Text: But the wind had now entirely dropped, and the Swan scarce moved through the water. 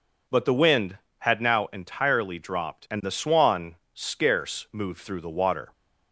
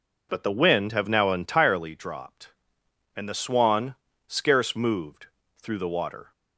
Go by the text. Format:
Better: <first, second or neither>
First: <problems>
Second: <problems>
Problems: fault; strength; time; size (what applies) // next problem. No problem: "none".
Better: first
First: pauses between "Swan" and "scarce"; slight; at 3.7 s; 0.18 s long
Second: says "have" for "had"; at 0.9 s // pauses between "Swan" and "scarce"; slight; at 3.9 s; 0.32 s long // pauses between "moved" and "through"; slight; at 5.2 s; 0.28 s long